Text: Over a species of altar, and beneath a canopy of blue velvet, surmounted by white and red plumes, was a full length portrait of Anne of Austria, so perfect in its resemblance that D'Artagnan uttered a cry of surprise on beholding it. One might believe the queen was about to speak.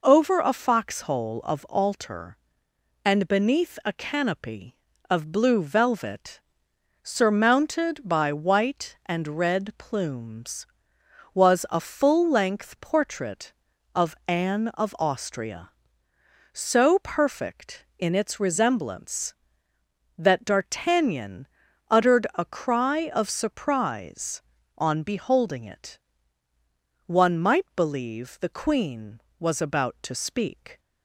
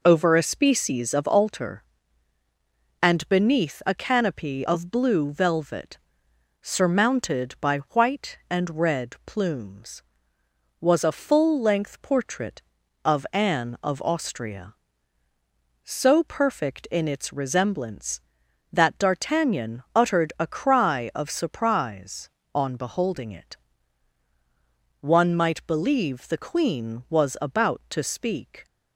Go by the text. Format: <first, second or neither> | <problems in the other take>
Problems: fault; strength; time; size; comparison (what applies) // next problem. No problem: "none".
second | says "foxhole" for "species"; at 0.5 s // pauses between "D'Artagnan" and "uttered"; at 21.4 s; 0.42 s long